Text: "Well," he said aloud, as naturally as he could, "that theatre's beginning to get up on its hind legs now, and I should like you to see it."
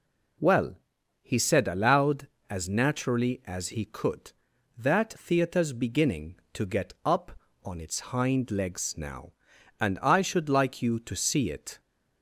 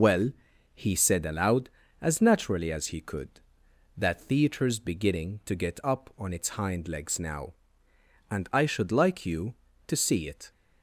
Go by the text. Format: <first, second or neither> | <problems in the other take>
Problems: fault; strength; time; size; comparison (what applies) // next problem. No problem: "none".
first | loses the start of "Well"; at 0.0 s; 80 ms